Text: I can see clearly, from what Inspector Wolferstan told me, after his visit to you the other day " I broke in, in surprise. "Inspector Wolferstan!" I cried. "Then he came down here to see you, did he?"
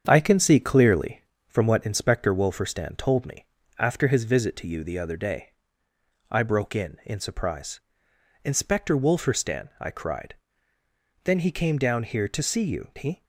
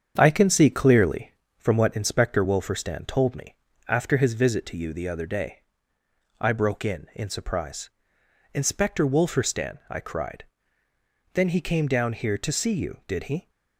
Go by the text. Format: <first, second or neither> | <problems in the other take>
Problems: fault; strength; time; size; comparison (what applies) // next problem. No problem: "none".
second | starts louder than the rest; strong; until 1.0 s; 7.5 dB; strong in the second // skips "did"; at 12.9 s